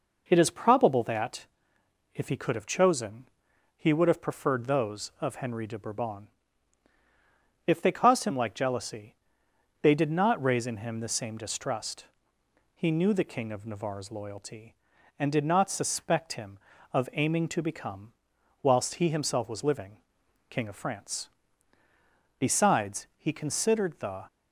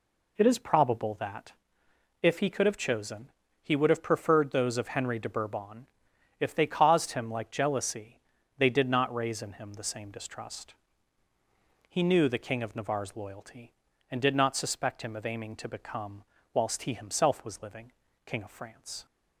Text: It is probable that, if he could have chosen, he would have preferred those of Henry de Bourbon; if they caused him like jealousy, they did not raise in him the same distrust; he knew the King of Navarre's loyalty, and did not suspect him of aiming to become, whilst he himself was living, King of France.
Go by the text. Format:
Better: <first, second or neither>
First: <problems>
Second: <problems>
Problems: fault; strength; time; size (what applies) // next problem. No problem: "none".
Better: second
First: goes on to say "Besides he considered the"; strong; from 22.3 s on; 1.9 s long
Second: none